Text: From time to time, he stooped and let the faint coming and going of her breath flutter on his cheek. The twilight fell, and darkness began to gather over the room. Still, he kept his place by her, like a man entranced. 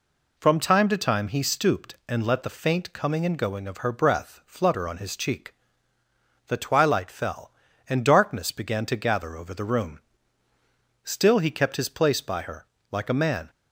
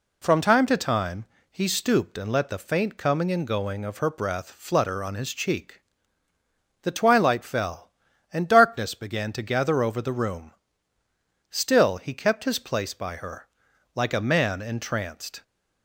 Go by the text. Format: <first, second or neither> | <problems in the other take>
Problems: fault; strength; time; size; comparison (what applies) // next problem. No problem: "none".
second | stops before "entranced"; at 13.4 s